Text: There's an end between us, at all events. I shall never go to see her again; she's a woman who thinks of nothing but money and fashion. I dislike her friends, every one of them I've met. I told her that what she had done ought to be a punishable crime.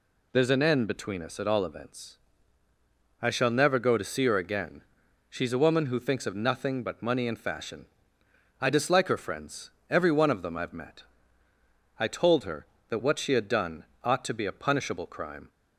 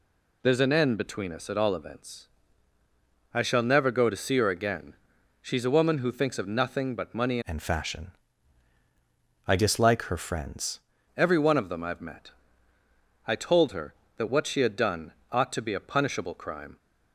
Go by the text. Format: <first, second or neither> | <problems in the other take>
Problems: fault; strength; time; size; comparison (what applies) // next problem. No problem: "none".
first | changes voice from "and" to "friends"; from 7.4 to 10.7 s; 3.3 s long // pauses between "done" and "ought"; slight; at 15.1 s; 0.18 s long; slight in the first